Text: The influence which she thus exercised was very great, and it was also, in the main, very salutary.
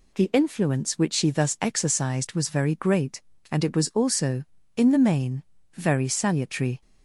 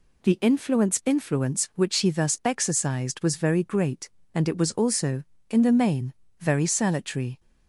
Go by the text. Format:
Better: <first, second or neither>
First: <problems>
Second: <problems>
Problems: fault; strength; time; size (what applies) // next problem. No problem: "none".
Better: first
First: none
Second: says "influence" twice; at 1.0 s